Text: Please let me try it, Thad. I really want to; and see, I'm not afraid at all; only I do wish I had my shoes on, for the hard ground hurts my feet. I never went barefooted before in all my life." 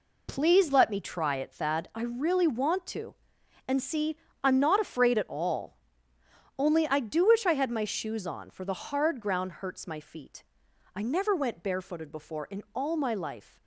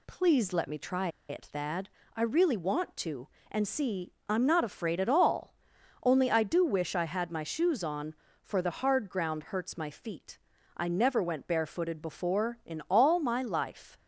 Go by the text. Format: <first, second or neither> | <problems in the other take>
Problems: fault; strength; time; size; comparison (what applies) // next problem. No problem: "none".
first | pauses between "try" and "it"; slight; at 1.0 s; 0.21 s long